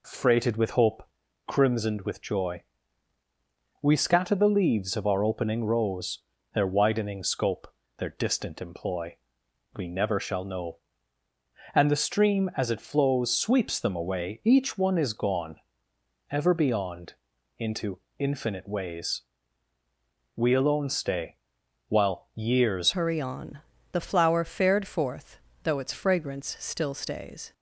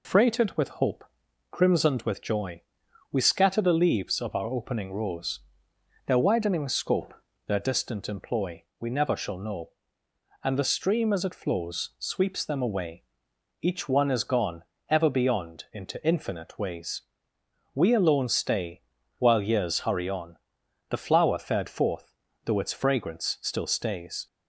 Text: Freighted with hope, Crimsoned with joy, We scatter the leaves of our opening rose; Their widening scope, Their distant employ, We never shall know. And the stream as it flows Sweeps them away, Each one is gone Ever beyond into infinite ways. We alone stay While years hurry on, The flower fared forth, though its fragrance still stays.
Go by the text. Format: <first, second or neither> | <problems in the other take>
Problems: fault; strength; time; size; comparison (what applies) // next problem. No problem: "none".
second | pauses between "gone" and "Ever"; noticeable; at 15.5 s; 0.74 s long; slight in the second // pauses between "beyond" and "into"; at 17.1 s; 0.44 s long // pauses between "into" and "infinite"; slight; at 17.9 s; 0.22 s long // pauses between "stay" and "While"; noticeable; at 21.3 s; 0.50 s long; slight in the second // changes voice at "hurry"; from 22.9 s on; 4.6 s long